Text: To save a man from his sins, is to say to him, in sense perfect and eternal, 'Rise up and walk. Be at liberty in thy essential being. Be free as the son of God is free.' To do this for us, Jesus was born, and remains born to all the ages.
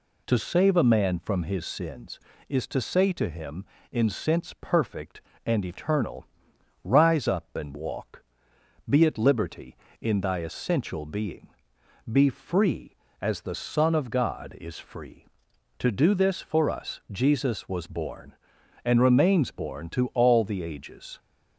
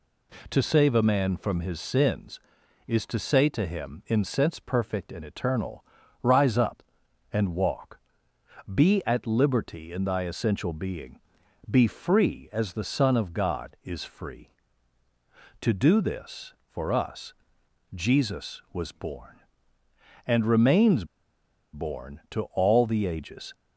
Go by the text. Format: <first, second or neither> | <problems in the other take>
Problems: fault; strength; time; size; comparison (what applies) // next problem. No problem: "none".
first | pauses between "remains" and "born"; noticeable; at 21.0 s; 0.68 s long